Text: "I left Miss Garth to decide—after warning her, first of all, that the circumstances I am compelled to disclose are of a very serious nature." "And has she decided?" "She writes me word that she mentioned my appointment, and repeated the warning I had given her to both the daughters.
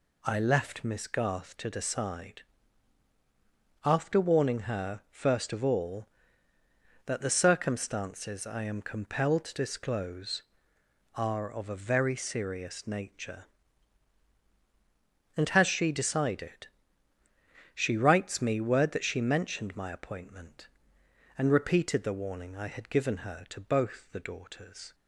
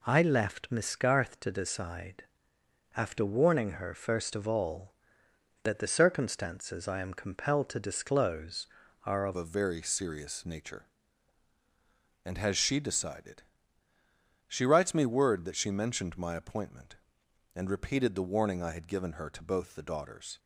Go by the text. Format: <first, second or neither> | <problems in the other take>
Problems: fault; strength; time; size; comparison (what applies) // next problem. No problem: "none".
first | changes voice at "a"; from 9.3 s on; 11.0 s long